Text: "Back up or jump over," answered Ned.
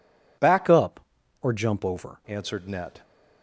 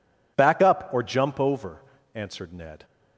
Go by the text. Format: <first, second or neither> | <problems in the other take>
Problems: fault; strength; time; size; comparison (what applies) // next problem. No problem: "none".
second | changes voice from "up" to "over"; from 0.6 to 2.2 s; 1.6 s long